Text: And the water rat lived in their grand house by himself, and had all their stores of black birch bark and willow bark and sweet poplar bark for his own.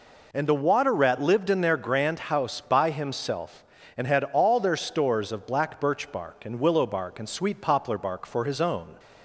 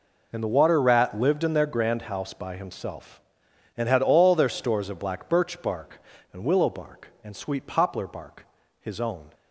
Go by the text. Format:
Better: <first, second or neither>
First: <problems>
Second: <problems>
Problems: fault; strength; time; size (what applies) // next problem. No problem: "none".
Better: first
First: none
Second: skips "for"; at 8.6 s